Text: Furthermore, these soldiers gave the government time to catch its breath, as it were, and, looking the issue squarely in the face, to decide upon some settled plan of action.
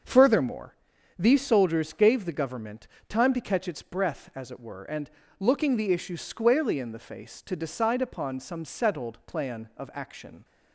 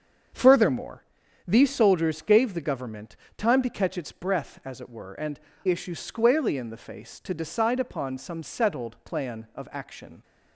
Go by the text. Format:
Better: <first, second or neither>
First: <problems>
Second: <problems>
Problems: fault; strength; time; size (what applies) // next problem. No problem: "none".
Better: first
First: starts louder than the rest; until 1.4 s; 6.5 dB // pauses between "government" and "time"; slight; at 2.8 s; 0.22 s long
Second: starts louder than the rest; until 1.7 s; 7 dB // pauses between "government" and "time"; slight; at 3.1 s; 0.22 s long // skips "looking the"; at 5.5 s